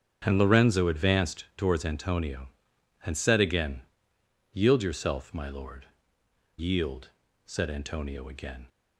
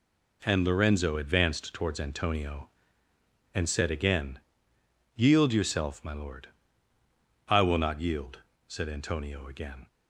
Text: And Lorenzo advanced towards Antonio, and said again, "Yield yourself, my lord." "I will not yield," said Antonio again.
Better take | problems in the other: second | starts louder than the rest; strong; until 1.2 s; 8 dB // skips "I will not"; at 6.2 s

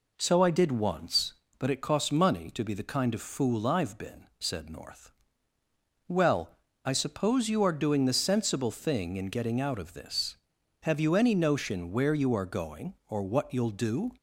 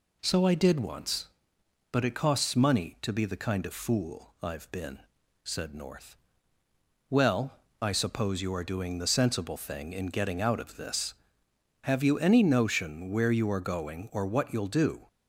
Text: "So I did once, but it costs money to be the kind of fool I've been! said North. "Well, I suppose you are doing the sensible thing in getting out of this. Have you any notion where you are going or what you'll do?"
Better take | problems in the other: neither | none

